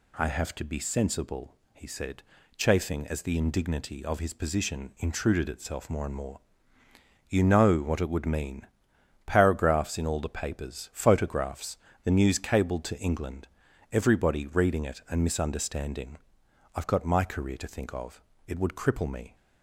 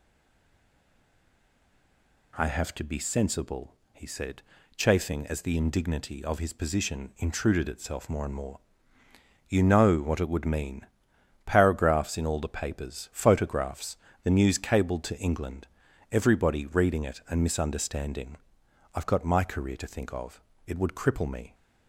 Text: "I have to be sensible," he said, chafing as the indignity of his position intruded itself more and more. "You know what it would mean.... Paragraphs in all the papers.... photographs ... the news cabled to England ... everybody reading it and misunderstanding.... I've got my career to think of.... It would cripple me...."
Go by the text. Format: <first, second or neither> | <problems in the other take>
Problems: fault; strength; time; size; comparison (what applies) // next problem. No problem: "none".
first | stays silent before the first word; until 2.3 s; 2.3 s long